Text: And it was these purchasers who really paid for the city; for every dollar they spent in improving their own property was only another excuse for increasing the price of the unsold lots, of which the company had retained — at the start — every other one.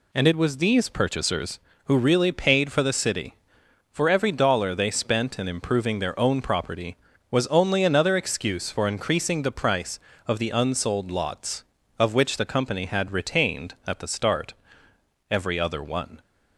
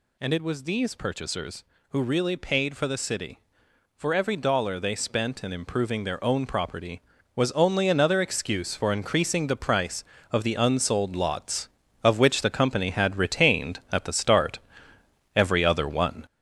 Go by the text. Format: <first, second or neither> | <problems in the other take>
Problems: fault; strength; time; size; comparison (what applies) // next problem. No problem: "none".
first | gets louder; noticeable; throughout; 5.5 dB